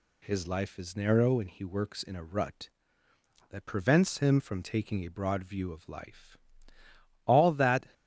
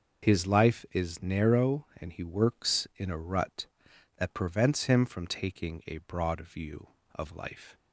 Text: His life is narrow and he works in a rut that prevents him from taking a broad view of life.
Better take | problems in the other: second | goes on to say "All that"; noticeable; from 7.2 s on; 0.66 s long

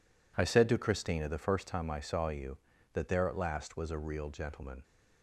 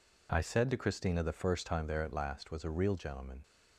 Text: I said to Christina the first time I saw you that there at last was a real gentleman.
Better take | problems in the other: first | skips "I saw you that"; at 1.8 s

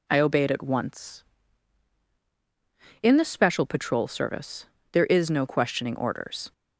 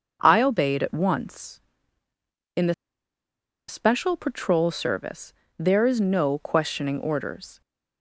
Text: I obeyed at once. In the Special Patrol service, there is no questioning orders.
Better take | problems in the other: first | starts louder than the rest; until 1.2 s; 6.5 dB // pauses between "the" and "Special"; noticeable; at 2.7 s; 0.94 s long

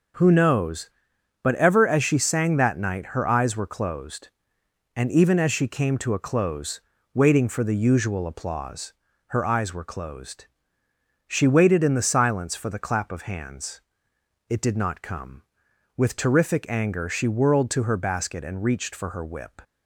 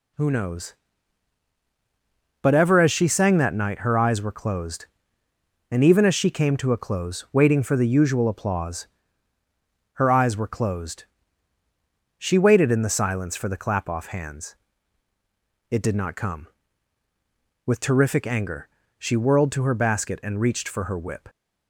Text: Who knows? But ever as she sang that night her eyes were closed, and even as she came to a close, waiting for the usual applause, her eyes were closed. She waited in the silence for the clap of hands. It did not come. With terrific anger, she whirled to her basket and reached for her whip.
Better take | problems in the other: first | says "off" for "of"; at 13.8 s

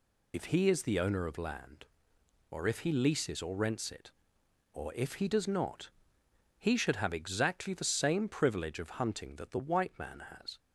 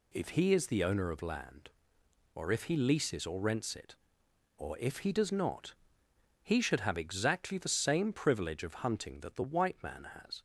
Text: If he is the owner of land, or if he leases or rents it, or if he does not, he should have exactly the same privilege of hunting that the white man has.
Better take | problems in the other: second | loses the start of "If"; at 0.3 s; 60 ms

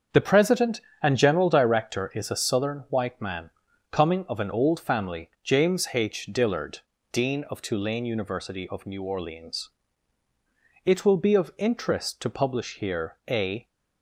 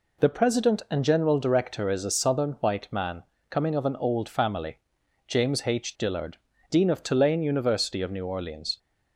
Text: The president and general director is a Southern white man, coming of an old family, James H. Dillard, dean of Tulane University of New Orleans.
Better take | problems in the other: second | starts louder than the rest; strong; until 1.3 s; 7 dB // goes on to say "It will be of interest to publish here a"; strong; from 10.8 s on; 2.8 s long

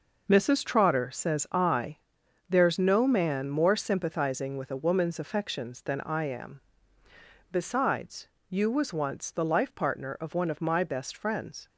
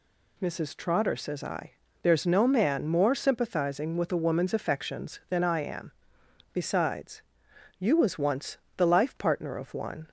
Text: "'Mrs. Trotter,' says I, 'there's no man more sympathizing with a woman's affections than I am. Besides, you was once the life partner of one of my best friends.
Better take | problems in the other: first | pauses between "once" and "the"; slight; at 8.5 s; 0.18 s long // stops before "of my best friends"; at 10.0 s

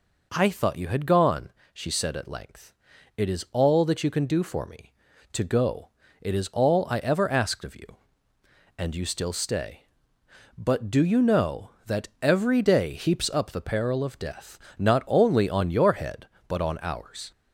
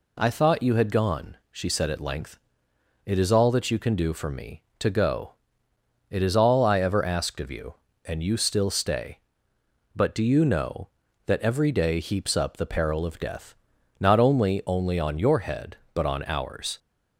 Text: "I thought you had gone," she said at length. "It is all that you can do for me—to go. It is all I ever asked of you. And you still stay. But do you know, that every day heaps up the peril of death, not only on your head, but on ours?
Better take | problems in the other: first | says "only" twice; at 14.6 s

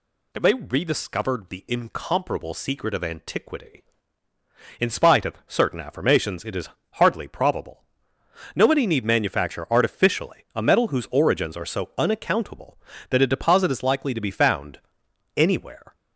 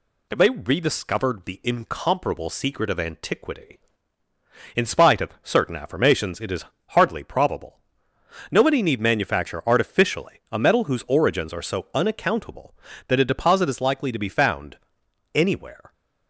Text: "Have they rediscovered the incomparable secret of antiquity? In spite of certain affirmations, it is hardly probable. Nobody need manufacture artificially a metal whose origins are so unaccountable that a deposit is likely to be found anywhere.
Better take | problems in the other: second | gets louder; throughout; 3.5 dB // pauses between "is" and "hardly"; slight; at 6.6 s; 0.24 s long; slight in the second // pauses between "found" and "anywhere"; noticeable; at 14.7 s; 0.58 s long; noticeable in the second

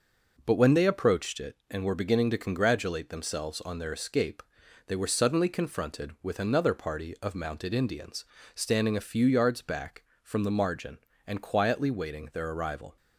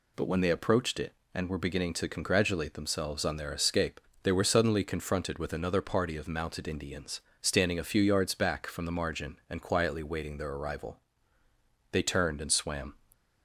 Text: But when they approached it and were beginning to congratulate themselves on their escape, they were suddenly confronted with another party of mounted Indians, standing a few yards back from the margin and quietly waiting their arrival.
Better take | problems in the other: first | goes on to say "They turned and swam"; noticeable; from 11.9 s on; 1.0 s long

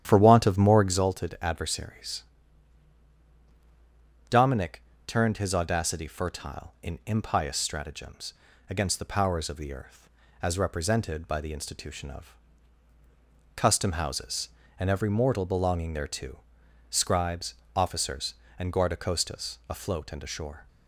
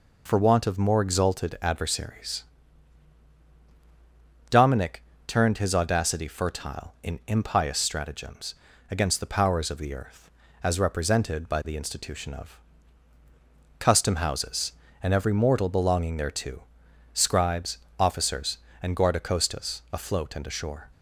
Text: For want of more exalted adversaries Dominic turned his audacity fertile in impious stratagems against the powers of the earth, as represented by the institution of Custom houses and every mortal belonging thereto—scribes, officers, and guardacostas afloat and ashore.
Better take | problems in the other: second | starts louder than the rest; strong; until 1.0 s; 10 dB // pauses between "adversaries" and "Dominic"; strong; at 2.2 s; 2.0 s long; strong in the second // pauses between "Dominic" and "turned"; slight; at 4.7 s; 0.28 s long; slight in the second // pauses between "stratagems" and "against"; slight; at 8.3 s; 0.36 s long; slight in the second // pauses between "of" and "Custom"; at 12.3 s; 1.2 s long; also in the second

